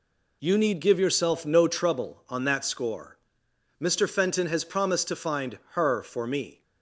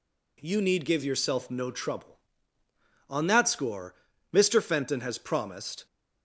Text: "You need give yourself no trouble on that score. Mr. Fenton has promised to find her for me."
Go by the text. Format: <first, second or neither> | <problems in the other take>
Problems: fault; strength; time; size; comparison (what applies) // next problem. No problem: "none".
first | stops before "to find her for me"; at 5.8 s